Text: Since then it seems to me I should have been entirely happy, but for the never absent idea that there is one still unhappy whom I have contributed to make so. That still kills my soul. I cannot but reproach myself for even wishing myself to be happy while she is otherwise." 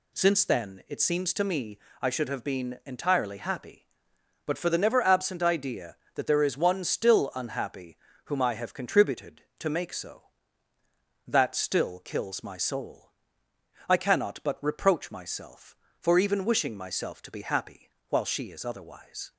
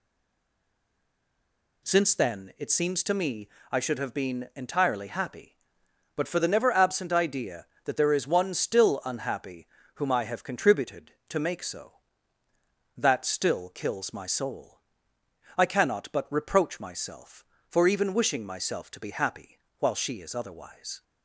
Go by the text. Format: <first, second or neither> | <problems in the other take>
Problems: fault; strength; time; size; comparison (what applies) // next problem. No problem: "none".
first | stays silent before the first word; noticeable; until 1.8 s; 1.8 s long // pauses between "me" and "I"; slight; at 3.4 s; 0.22 s long; slight in the first // pauses between "unhappy" and "whom"; slight; at 9.6 s; 0.30 s long; slight in the first // pauses between "happy" and "while"; slight; at 19.5 s; 0.20 s long; slight in the first